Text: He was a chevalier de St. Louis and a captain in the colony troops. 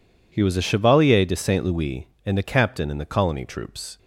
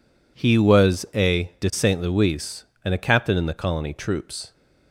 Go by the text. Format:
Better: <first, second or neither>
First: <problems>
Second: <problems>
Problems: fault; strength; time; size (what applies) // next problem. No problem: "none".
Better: first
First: none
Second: skips "chevalier"; at 1.5 s